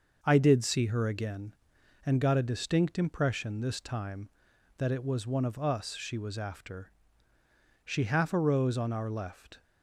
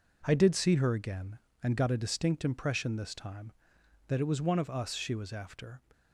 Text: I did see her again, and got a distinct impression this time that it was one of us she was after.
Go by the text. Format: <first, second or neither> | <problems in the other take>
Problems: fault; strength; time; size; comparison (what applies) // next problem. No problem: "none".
second | starts louder than the rest; until 1.2 s; 6 dB // goes on to say "She half arose on our left"; strong; from 7.8 s on; 1.7 s long